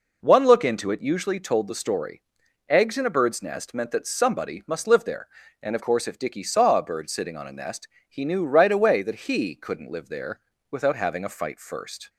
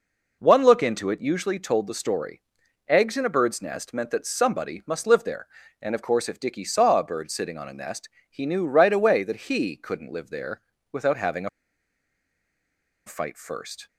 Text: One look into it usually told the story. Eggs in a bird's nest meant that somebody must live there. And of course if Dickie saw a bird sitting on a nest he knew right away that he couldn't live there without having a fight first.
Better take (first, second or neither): first